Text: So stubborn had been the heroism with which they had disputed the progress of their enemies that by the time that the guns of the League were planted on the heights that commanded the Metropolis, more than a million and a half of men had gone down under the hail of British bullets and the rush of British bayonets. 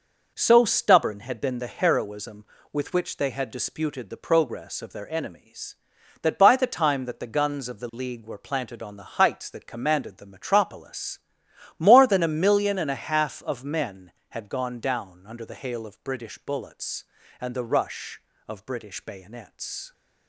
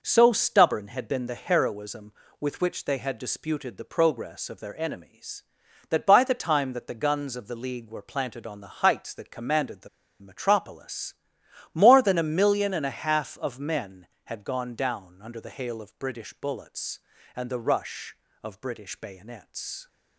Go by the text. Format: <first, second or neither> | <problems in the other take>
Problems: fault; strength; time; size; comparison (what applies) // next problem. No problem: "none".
first | pauses between "the" and "Metropolis"; slight; at 9.8 s; 0.32 s long